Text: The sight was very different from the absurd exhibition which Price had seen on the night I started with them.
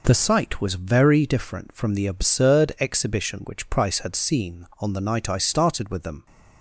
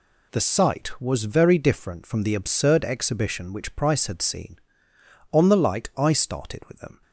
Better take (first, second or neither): first